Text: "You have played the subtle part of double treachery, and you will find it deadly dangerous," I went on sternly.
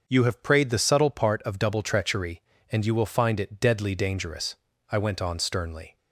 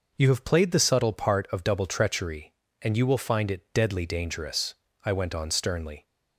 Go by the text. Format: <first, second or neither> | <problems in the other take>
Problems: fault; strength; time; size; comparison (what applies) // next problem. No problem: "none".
second | starts louder than the rest; until 1.0 s; 6.5 dB // says "prayed" for "played"; at 0.4 s